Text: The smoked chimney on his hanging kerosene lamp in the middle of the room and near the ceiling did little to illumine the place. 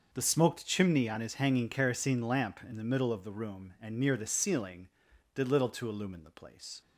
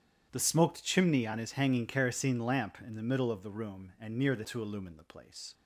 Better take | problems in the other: first | starts louder than the rest; strong; until 1.3 s; 10 dB // skips "ceiling did little"; at 4.4 s

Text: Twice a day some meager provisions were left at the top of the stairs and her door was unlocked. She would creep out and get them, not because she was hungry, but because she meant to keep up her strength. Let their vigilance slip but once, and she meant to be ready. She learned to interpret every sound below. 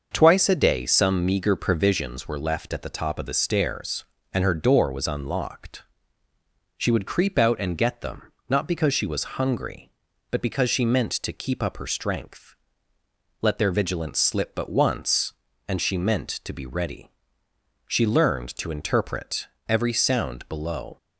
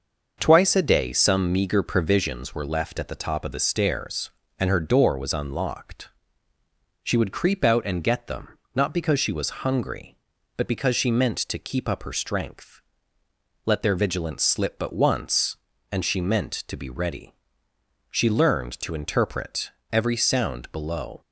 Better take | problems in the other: neither | starts louder than the rest; the same in both // pauses between "interpret" and "every"; slight; the same in both

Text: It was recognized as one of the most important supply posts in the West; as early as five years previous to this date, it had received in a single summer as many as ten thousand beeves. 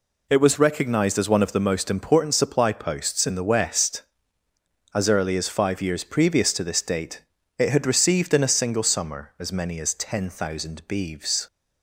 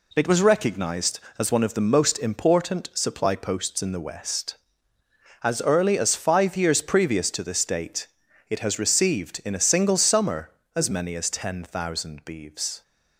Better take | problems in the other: first | says "has" for "had"; at 8.5 s

